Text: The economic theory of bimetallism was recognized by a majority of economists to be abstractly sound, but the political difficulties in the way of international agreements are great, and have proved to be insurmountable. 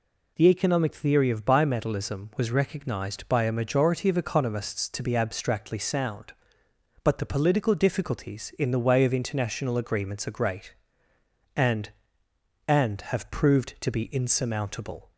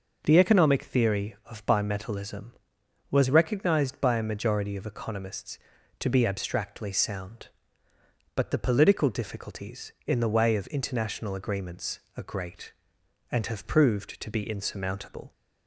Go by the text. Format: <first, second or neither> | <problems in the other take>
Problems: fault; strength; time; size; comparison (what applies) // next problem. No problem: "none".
second | says "and" twice; at 12.6 s